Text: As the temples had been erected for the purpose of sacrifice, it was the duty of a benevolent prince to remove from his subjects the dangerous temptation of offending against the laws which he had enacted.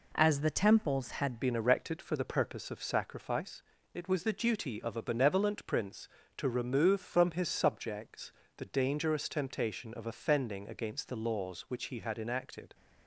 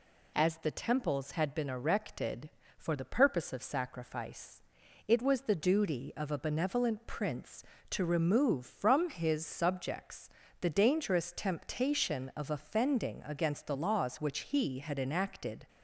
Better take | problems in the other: second | changes voice at "been"; from 1.4 s on; 11.3 s long // pauses between "subjects" and "the"; slight; at 8.3 s; 0.26 s long; slight in the second

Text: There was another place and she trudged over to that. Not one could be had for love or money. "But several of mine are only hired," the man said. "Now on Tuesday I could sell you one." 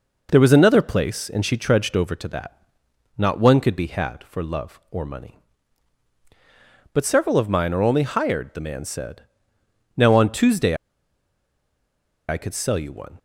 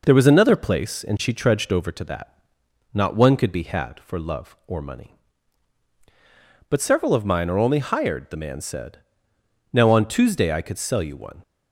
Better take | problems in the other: second | pauses between "Tuesday" and "I"; strong; at 10.7 s; 1.5 s long

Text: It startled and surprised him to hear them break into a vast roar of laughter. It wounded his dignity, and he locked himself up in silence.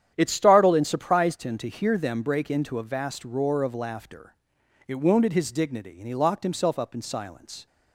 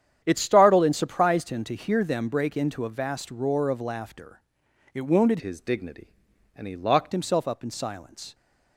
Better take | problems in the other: first | starts louder than the rest; strong; until 1.2 s; 9.5 dB; strong in the first // changes voice from "his" to "locked"; from 5.4 to 7.1 s; 1.7 s long

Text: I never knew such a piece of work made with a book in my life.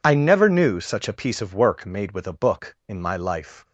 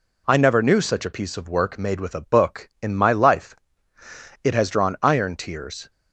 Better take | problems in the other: first | goes on to say "It has drawn iron tears"; from 4.4 s on; 1.4 s long

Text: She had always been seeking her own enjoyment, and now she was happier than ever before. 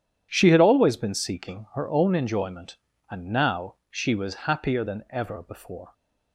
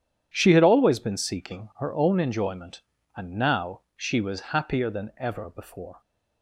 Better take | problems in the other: neither | starts louder than the rest; strong; the same in both

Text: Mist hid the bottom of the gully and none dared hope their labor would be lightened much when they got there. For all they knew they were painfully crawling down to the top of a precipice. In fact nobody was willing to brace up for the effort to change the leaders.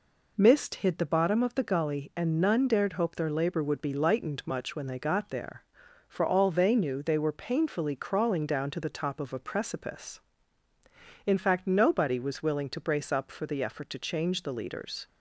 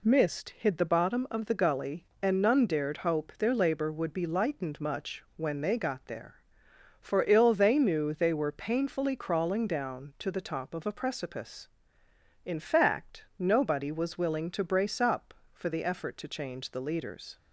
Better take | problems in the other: first | says "ill" for "all"; at 7.2 s // pauses between "fact" and "nobody"; slight; at 13.2 s; 0.16 s long

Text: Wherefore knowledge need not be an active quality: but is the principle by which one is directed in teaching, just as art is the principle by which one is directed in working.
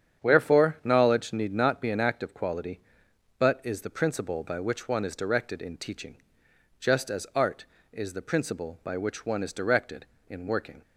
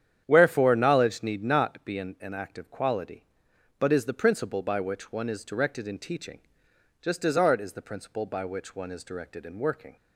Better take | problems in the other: first | starts louder than the rest; strong; until 1.2 s; 9 dB; strong in the first // says "an" twice; at 2.2 s

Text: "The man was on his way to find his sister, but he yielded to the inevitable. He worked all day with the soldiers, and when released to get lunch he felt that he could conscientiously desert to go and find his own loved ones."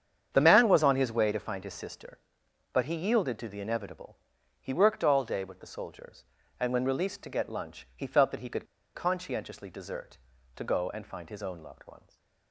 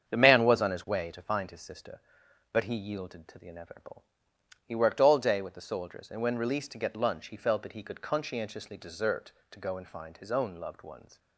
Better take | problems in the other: second | starts louder than the rest; strong; until 1.3 s; 8.5 dB; strong in the second // pauses between "could" and "conscientiously"; slight; at 8.6 s; 0.30 s long // stays silent after the last word; slight; from 11.9 s on; 0.6 s long

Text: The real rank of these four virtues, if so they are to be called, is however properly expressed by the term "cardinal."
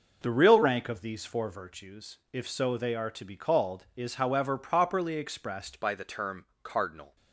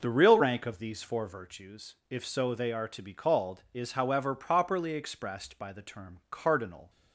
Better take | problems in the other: second | changes voice at "by"; from 5.8 s on; 1.3 s long // pauses between "term" and "cardinal"; slight; at 6.4 s; 0.16 s long

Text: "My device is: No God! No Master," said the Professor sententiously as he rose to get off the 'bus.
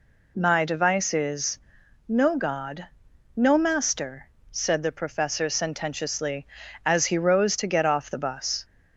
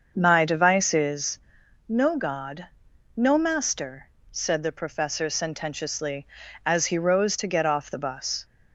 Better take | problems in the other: first | starts louder than the rest; until 1.2 s; 6.5 dB

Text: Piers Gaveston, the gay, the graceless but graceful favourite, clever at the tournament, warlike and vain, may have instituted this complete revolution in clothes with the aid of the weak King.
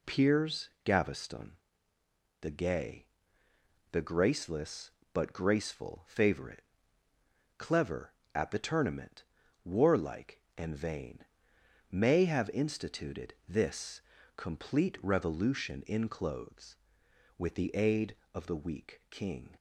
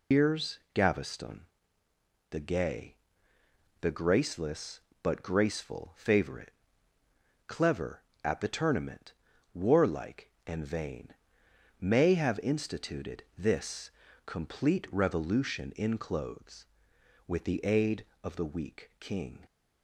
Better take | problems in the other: first | loses the start of "Piers"; at 0.1 s; 155 ms // pauses between "this" and "complete"; slight; at 13.9 s; 0.34 s long; slight in the first

